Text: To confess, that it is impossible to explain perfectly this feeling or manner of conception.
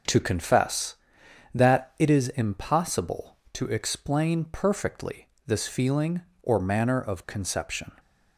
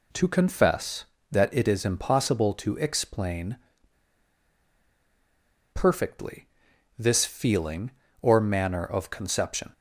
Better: first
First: pauses between "perfectly" and "this"; slight; at 5.2 s; 0.20 s long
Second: pauses between "explain" and "perfectly"; strong; at 3.5 s; 2.1 s long // pauses between "perfectly" and "this"; noticeable; at 6.4 s; 0.50 s long

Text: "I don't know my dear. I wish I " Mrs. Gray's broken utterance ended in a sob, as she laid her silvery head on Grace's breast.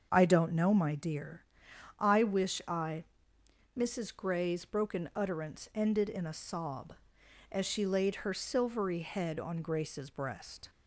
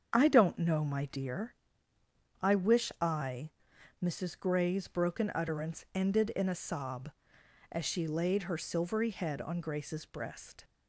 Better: neither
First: starts louder than the rest; until 1.1 s; 6.5 dB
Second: starts louder than the rest; until 1.1 s; 7 dB

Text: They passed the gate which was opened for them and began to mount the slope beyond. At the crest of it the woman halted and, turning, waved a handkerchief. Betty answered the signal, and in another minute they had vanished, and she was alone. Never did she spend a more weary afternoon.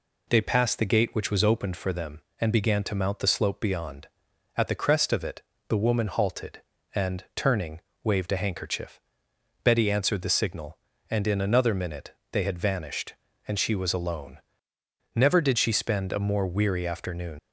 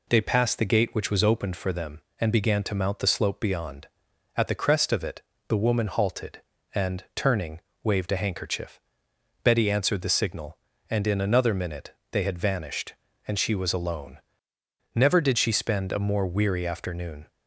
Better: second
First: pauses between "it" and "the"; slight; at 5.4 s; 0.28 s long // pauses between "minute" and "they"; slight; at 12.1 s; 0.18 s long // leaves "afternoon" unfinished; at 17.3 s; 95 ms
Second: pauses between "it" and "the"; slight; at 5.2 s; 0.28 s long // pauses between "minute" and "they"; slight; at 11.9 s; 0.18 s long

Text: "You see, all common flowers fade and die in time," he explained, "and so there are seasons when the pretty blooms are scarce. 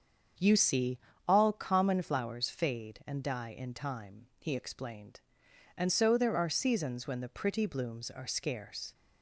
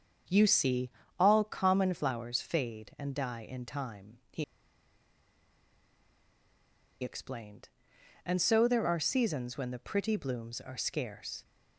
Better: first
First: starts louder than the rest; until 1.7 s; 7 dB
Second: starts louder than the rest; until 1.5 s; 7 dB // pauses between "he" and "explained"; strong; at 4.4 s; 2.5 s long

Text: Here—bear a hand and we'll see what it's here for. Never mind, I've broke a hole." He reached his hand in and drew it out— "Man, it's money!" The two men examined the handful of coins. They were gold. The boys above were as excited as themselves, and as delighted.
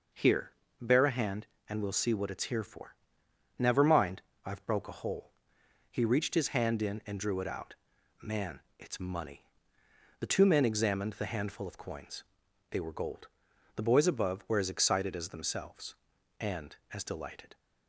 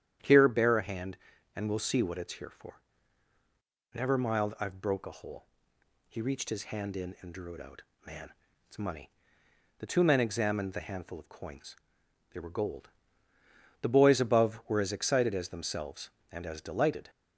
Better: first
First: none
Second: starts louder than the rest; strong; until 1.5 s; 9.5 dB // says "mild" for "mind"; at 4.1 s

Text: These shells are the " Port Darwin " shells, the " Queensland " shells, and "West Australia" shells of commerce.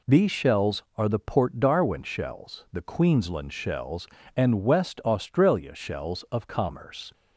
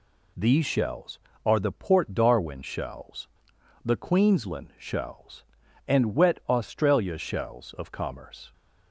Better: first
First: none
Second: says "Wet" for "West"; at 6.1 s

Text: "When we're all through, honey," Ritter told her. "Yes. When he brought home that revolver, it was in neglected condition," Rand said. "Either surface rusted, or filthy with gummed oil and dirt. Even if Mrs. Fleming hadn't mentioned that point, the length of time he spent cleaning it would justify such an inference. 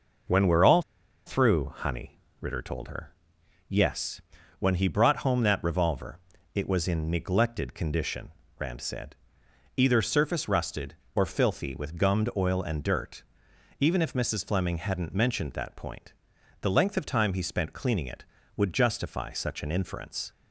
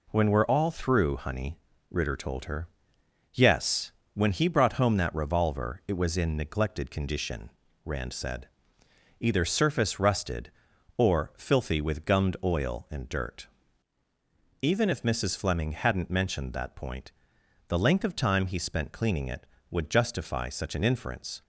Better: second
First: pauses between "all" and "through"; at 0.8 s; 0.44 s long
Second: none

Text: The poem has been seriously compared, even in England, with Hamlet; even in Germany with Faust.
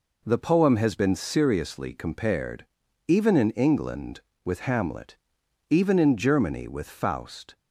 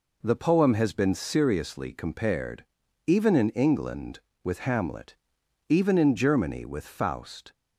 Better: neither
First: none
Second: none

